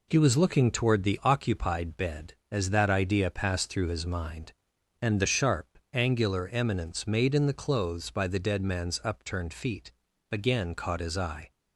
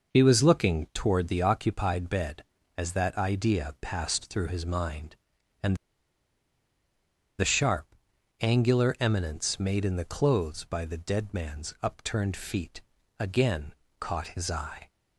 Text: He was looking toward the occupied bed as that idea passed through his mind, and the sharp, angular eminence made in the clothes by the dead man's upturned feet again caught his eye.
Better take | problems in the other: first | pauses between "and" and "the"; strong; at 5.7 s; 1.6 s long // pauses between "feet" and "again"; slight; at 12.8 s; 0.36 s long; also in the first // pauses between "again" and "caught"; slight; at 13.7 s; 0.28 s long

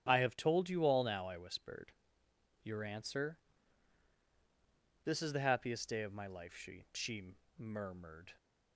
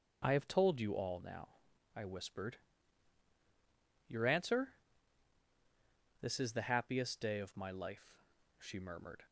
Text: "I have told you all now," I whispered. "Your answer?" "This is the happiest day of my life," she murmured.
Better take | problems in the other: second | starts louder than the rest; strong; until 1.0 s; 8.5 dB // says "she" twice; at 6.9 s

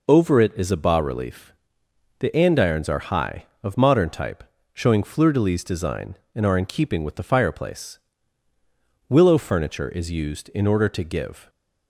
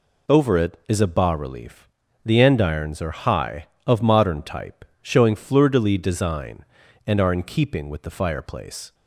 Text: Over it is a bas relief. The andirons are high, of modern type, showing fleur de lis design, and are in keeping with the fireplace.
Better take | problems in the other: second | goes on to say "Willow furniture is used in order to give"; strong; from 9.0 s on; 2.4 s long

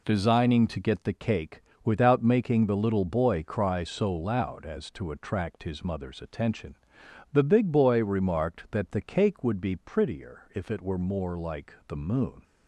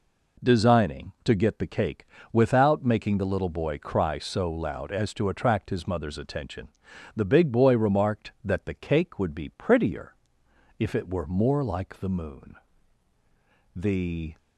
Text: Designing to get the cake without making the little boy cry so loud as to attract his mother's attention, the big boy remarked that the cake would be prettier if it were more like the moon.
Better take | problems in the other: first | pauses between "cake" and "without"; slight; at 2.0 s; 0.26 s long; slight in the first // pauses between "prettier" and "if"; noticeable; at 10.1 s; 0.64 s long // goes on to say "The"; noticeable; from 13.7 s on; 0.62 s long

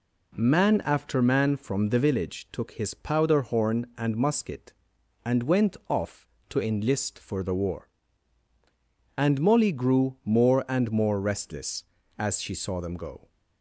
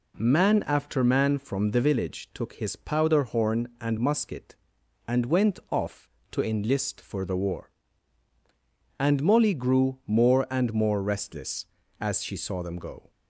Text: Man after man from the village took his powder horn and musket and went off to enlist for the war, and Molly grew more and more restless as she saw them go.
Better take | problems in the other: neither | none

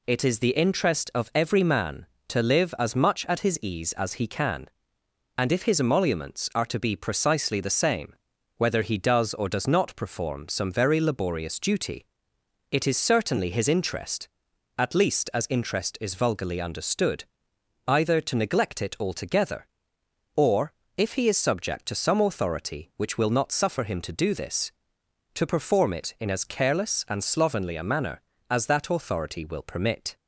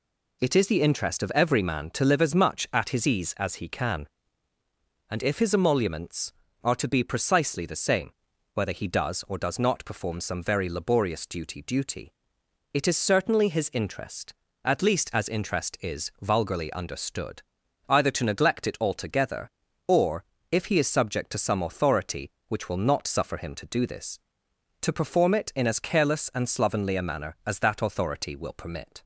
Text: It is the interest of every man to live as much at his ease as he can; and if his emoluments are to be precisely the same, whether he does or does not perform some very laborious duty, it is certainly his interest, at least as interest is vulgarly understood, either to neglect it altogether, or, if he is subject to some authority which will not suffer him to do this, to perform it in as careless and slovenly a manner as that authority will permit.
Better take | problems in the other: first | says "duty" twice; at 11.6 s

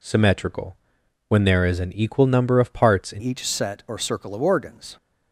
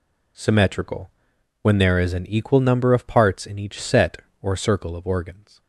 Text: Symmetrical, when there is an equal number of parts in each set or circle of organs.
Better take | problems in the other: second | changes voice at "each"; from 3.1 s on; 1.8 s long

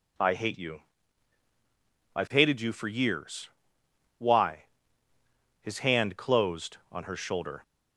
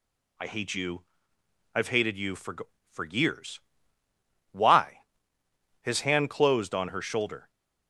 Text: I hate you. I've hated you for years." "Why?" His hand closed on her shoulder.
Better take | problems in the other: first | says "for" twice; at 2.9 s

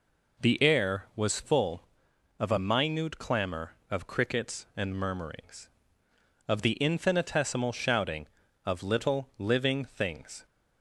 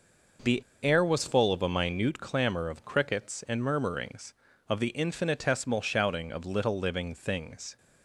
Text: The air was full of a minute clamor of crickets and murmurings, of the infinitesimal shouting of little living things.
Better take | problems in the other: first | pauses between "The" and "air"; slight; at 0.6 s; 0.19 s long

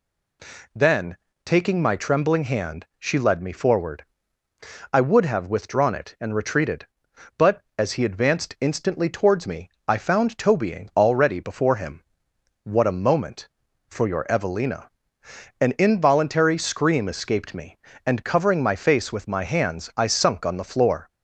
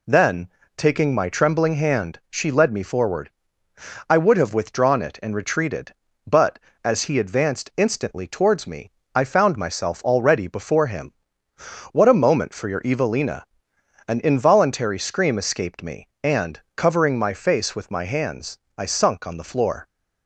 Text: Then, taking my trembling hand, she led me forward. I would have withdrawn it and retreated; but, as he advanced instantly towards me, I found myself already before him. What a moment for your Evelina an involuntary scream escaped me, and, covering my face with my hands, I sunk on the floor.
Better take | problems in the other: second | says "tobying" for "myself"; at 10.3 s // pauses between "Evelina" and "an"; noticeable; at 14.8 s; 0.72 s long; noticeable in the second

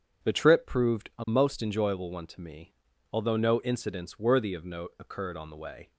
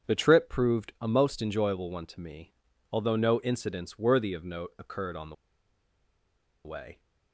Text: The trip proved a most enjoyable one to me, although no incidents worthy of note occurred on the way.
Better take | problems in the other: first | starts louder than the rest; strong; until 1.1 s; 7.5 dB; strong in the first // pauses between "the" and "way"; strong; at 5.3 s; 1.3 s long

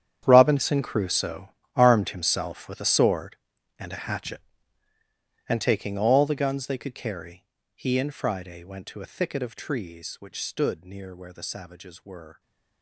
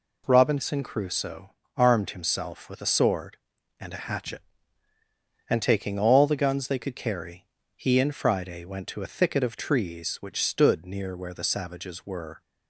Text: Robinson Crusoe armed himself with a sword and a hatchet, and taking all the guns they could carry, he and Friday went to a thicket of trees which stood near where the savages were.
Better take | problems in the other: second | gets quieter; strong; throughout; 16.5 dB // pauses between "Crusoe" and "armed"; slight; at 1.4 s; 0.26 s long; slight in the second

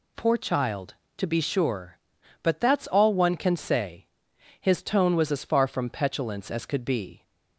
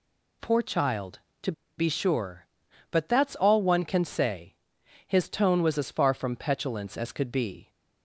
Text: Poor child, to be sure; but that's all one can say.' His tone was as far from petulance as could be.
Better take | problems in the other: first | pauses between "to" and "be"; slight; at 1.5 s; 0.26 s long

